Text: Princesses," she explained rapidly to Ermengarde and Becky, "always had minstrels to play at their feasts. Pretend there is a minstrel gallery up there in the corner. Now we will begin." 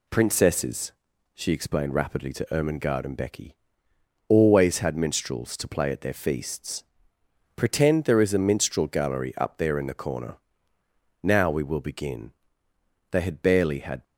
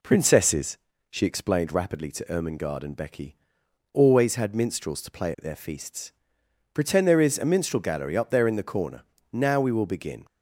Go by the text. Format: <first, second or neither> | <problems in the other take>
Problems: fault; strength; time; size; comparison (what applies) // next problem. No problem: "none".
second | goes on to say "They had barely had"; noticeable; from 13.1 s on; 0.92 s long